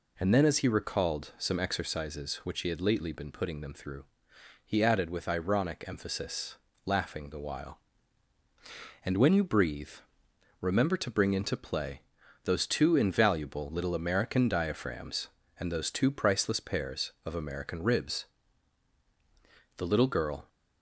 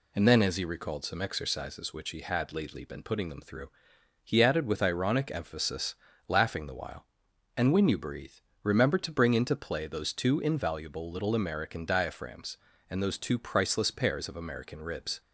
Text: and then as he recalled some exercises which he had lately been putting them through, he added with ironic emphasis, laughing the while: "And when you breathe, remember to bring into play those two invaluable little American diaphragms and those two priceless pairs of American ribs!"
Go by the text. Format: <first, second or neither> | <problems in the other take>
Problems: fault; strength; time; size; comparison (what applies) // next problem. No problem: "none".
second | pauses between "play" and "those"; noticeable; at 11.9 s; 0.46 s long // goes on to say "The little girl"; noticeable; from 19.7 s on; 0.72 s long